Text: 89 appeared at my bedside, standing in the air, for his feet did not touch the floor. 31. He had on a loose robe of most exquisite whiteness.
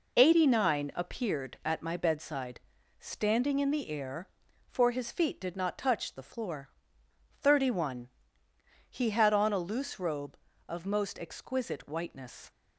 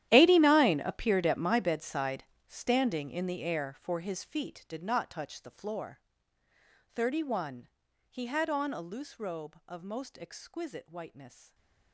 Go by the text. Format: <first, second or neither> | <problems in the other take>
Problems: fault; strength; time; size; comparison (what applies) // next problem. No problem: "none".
first | gets quieter; strong; throughout; 19 dB // stays silent after the last word; slight; from 11.2 s on; 0.7 s long